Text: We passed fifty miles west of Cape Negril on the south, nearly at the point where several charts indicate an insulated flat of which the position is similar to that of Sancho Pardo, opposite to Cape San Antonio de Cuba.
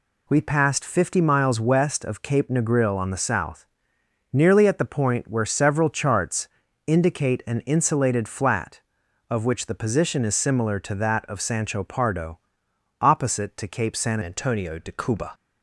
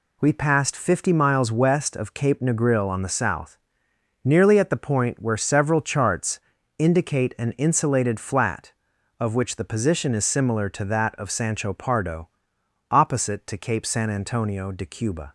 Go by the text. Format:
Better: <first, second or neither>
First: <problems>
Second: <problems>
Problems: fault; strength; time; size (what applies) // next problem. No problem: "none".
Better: second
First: pauses between "charts" and "indicate"; slight; at 6.4 s; 0.36 s long // changes voice at "Antonio"; from 14.2 s on; 1.1 s long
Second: pauses between "charts" and "indicate"; slight; at 6.4 s; 0.36 s long